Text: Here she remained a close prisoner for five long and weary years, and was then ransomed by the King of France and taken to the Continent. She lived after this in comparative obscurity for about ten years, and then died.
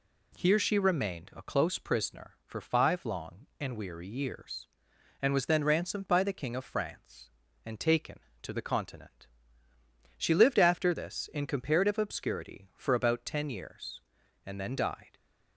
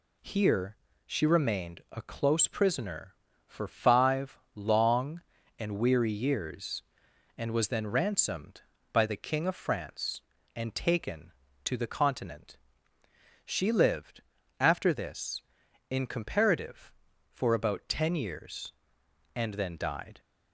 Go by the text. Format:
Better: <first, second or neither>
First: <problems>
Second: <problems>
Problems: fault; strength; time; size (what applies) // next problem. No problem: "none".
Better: first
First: none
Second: pauses between "Here" and "she"; slight; at 0.7 s; 0.30 s long // pauses between "five" and "long"; slight; at 4.3 s; 0.16 s long // pauses between "lived" and "after"; at 14.2 s; 0.38 s long // skips "obscurity"; at 17.1 s